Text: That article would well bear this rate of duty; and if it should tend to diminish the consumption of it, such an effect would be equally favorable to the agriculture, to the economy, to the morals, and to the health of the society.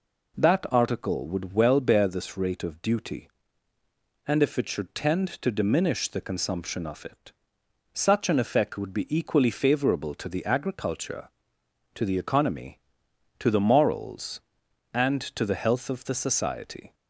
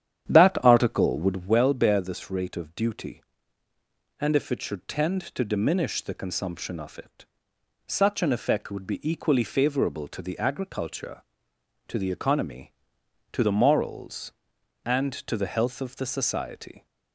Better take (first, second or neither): first